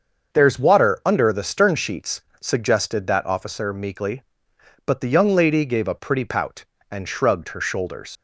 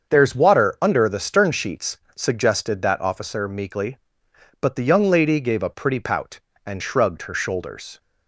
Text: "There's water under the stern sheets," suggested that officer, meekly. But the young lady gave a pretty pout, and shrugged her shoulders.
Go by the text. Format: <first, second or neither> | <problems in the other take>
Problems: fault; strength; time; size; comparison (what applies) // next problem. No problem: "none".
second | starts louder than the rest; until 1.4 s; 6.5 dB; also in the second // leaves "shoulders" unfinished; at 8.1 s; 115 ms